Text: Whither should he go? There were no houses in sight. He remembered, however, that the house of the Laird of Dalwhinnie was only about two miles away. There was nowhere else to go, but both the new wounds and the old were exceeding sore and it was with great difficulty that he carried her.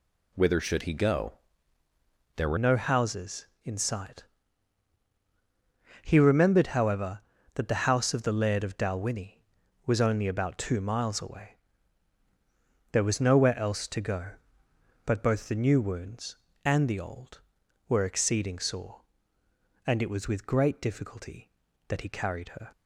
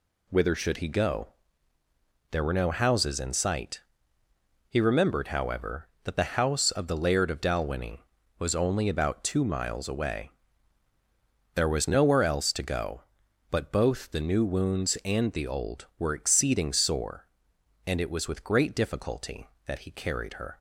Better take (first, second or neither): second